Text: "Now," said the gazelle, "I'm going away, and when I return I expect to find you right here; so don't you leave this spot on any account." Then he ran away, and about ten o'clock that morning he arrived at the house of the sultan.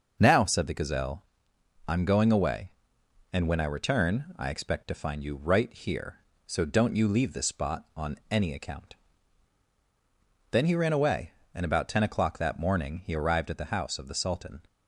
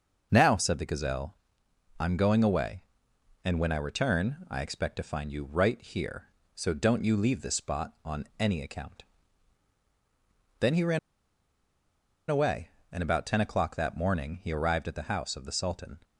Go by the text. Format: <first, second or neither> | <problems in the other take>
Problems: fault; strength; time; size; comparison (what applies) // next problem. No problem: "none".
first | pauses between "ran" and "away"; strong; at 10.9 s; 1.3 s long